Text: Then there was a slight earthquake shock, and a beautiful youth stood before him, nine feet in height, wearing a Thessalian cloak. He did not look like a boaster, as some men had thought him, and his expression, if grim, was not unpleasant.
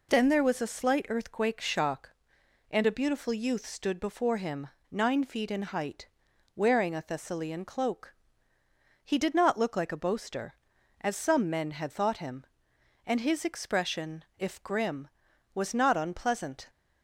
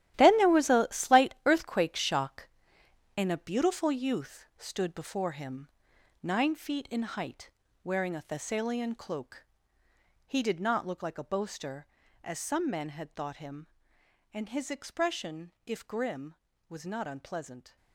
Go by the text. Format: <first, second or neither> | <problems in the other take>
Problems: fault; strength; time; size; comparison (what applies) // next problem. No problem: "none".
first | gets quieter; strong; throughout; 12.5 dB